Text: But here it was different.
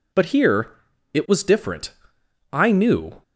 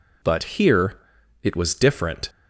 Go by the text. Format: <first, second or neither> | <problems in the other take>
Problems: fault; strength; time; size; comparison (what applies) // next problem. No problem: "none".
second | pauses between "here" and "it"; at 0.7 s; 0.42 s long; also in the second // goes on to say "I knew"; noticeable; from 2.5 s on; 0.70 s long